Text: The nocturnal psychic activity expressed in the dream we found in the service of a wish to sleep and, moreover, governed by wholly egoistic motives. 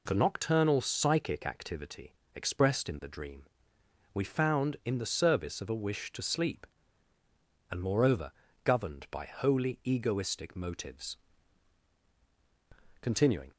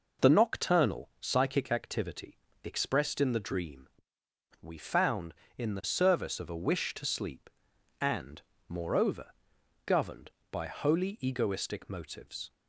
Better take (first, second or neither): second